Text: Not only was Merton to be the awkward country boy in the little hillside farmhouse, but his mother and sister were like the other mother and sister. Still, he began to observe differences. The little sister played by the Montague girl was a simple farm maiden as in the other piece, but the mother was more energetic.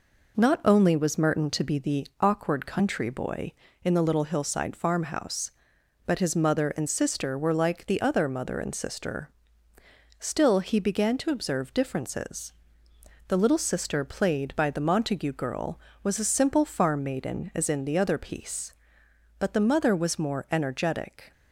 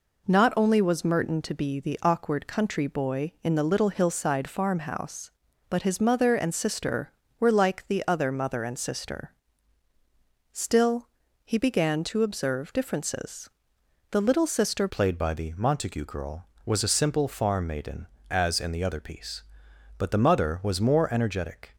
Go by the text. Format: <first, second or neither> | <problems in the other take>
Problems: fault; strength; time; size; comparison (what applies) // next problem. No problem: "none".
first | changes voice at "played"; from 14.8 s on; 6.9 s long